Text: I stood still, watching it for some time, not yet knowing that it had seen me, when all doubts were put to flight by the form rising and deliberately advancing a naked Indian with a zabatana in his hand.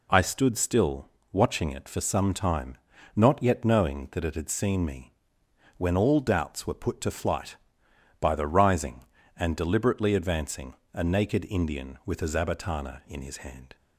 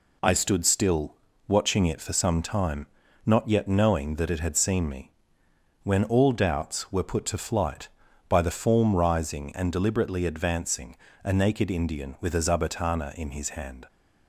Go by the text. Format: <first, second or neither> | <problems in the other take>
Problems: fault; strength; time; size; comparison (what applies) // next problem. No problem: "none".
second | skips "form"; at 8.4 s // pauses between "advancing" and "a"; slight; at 10.7 s; 0.22 s long; slight in the second